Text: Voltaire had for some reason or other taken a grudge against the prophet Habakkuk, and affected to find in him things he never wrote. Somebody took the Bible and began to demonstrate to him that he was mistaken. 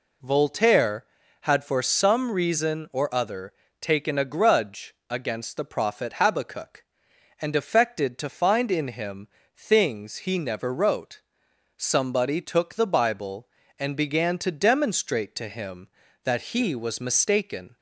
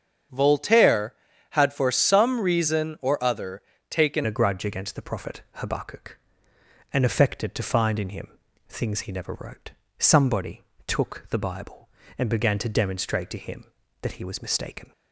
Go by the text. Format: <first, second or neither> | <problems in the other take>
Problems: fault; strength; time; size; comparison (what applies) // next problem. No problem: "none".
first | starts louder than the rest; strong; until 1.6 s; 7.5 dB // pauses between "other" and "taken"; slight; at 3.6 s; 0.28 s long; slight in the first // changes voice at "a"; from 4.2 s on; 10.7 s long // pauses between "him" and "things"; at 8.2 s; 0.42 s long; slight in the first // pauses between "Somebody" and "took"; slight; at 10.6 s; 0.22 s long